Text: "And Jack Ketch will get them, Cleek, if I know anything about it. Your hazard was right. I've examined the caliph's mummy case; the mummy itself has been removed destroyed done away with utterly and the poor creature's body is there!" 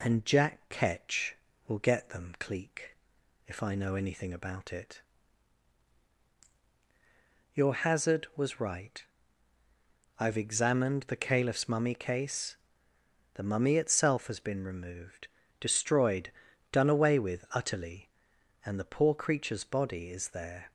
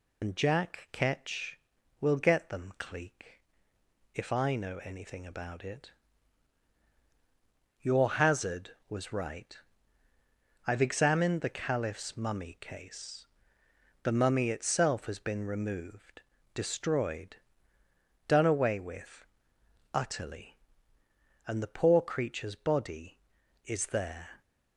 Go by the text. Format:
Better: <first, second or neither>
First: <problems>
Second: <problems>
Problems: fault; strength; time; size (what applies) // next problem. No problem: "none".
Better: first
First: pauses between "removed" and "destroyed"; slight; at 15.2 s; 0.32 s long // pauses between "destroyed" and "done"; at 16.3 s; 0.40 s long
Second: loses the start of "And"; at 0.2 s; 50 ms // pauses between "removed" and "destroyed"; slight; at 16.2 s; 0.32 s long // pauses between "destroyed" and "done"; noticeable; at 17.3 s; 0.90 s long // pauses between "with" and "utterly"; noticeable; at 19.2 s; 0.70 s long